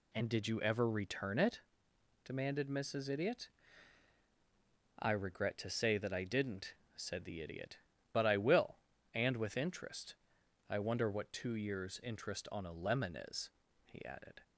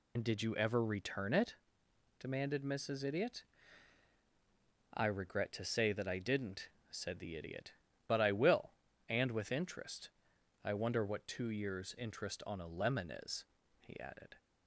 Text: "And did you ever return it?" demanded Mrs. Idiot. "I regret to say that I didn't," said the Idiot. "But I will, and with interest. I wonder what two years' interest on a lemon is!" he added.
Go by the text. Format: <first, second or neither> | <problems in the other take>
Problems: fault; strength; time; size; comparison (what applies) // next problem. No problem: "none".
first | loses the start of "And"; at 0.1 s; 70 ms